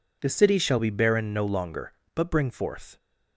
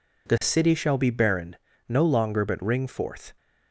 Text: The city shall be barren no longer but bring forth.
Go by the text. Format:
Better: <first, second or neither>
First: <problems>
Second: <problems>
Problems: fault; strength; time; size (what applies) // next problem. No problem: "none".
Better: first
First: none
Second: pauses between "barren" and "no"; slight; at 1.5 s; 0.32 s long // says "ring" for "bring"; at 2.6 s